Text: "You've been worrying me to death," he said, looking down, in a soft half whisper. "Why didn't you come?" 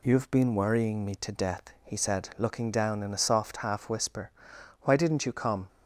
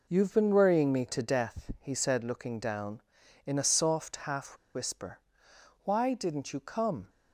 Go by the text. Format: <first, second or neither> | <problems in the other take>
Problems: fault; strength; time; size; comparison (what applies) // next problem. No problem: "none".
first | pauses between "half" and "whisper"; slight; at 4.5 s; 0.19 s long